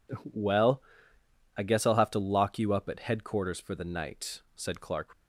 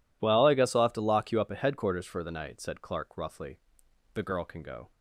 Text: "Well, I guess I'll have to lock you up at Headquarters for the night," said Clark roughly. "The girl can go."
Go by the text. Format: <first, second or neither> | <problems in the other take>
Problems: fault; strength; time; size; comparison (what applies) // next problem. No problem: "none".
second | stops before "roughly The girl can go"; at 5.1 s